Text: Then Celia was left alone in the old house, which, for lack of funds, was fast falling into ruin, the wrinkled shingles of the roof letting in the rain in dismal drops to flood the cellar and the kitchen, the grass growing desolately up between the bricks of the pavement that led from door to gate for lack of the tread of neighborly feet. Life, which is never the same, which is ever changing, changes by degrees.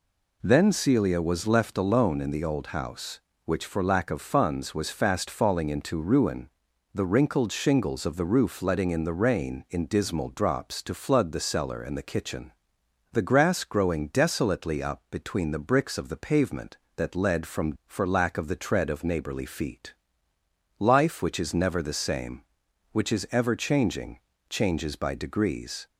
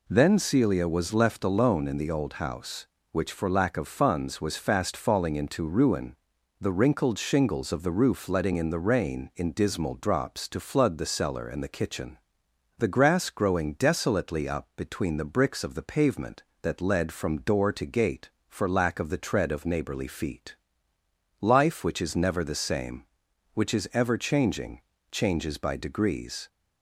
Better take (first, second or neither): second